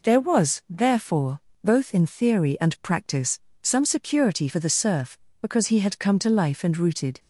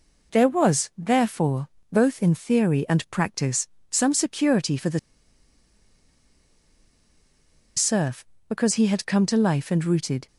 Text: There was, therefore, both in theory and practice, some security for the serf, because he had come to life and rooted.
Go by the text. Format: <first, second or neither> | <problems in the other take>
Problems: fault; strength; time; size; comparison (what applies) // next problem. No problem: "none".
first | pauses between "the" and "serf"; strong; at 4.9 s; 2.7 s long